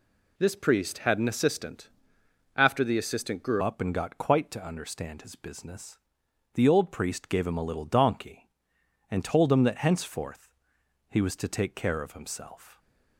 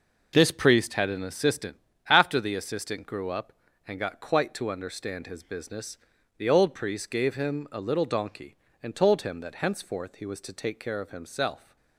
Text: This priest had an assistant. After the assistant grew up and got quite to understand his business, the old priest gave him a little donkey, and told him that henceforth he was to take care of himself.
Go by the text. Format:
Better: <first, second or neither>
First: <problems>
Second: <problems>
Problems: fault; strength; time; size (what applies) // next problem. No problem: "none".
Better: second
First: changes voice at "up"; from 3.5 s on; 9.2 s long // pauses between "henceforth" and "he"; noticeable; at 10.5 s; 0.54 s long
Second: none